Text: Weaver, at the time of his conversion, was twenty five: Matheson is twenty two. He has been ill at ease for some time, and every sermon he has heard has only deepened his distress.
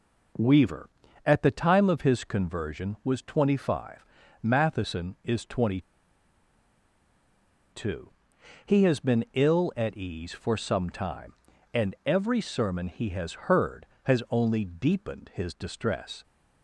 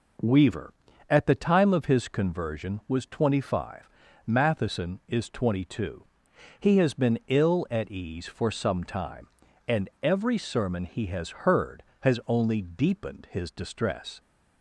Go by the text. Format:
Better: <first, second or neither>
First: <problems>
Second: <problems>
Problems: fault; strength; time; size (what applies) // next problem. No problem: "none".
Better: second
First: pauses between "twenty" and "two"; strong; at 5.7 s; 1.9 s long // pauses between "has" and "heard"; slight; at 13.3 s; 0.18 s long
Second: pauses between "has" and "heard"; slight; at 11.2 s; 0.18 s long